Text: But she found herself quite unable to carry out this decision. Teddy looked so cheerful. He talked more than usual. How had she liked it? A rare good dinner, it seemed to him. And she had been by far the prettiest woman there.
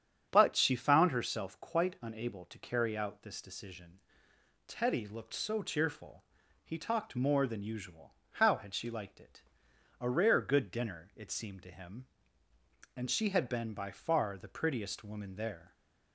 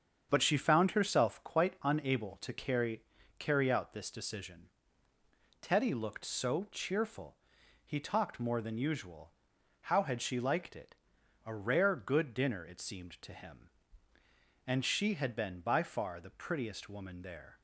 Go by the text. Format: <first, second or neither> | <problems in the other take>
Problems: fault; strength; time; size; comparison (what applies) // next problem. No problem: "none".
first | starts louder than the rest; strong; until 1.3 s; 7.5 dB; strong in the first // says "carry" twice; at 3.3 s